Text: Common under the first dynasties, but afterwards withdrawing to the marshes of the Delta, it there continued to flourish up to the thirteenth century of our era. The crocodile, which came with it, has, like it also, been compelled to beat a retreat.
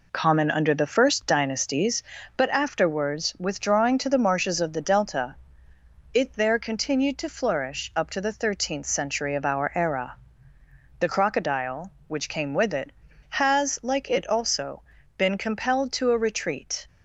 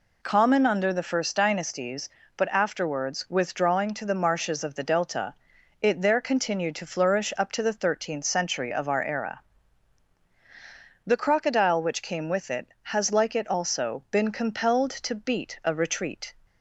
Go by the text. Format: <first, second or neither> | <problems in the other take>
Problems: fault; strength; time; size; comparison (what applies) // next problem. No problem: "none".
second | skips "beat"; at 16.1 s